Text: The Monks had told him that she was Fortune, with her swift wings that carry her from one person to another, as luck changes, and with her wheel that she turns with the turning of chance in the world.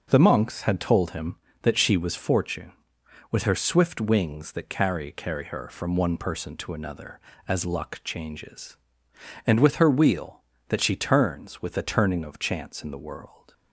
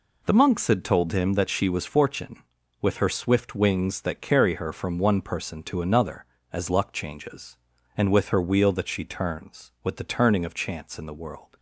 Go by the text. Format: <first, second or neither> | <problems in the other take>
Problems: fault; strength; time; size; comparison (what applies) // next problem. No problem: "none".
second | says "carry" twice; at 5.1 s